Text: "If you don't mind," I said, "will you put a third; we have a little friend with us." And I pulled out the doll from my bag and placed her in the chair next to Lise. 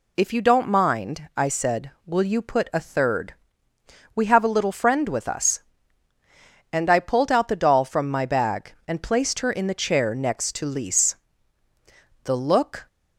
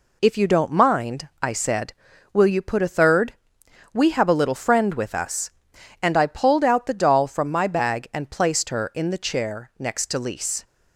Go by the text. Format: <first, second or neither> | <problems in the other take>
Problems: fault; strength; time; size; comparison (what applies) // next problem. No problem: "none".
second | goes on to say "The look"; noticeable; from 12.2 s on; 0.64 s long